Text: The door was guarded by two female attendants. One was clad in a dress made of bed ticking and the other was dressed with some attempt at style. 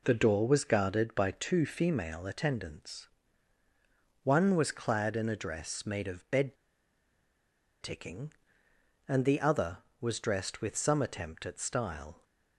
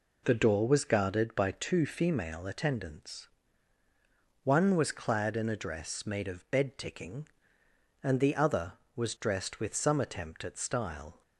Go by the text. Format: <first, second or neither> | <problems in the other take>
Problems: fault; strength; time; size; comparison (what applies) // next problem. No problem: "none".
second | pauses between "bed" and "ticking"; strong; at 6.5 s; 1.2 s long